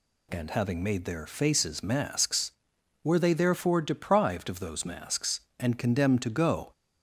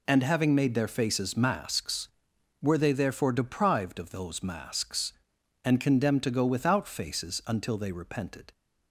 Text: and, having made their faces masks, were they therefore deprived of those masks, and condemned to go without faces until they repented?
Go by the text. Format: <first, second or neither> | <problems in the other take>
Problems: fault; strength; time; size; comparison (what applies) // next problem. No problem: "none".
second | stops before "without faces until they repented"; at 6.7 s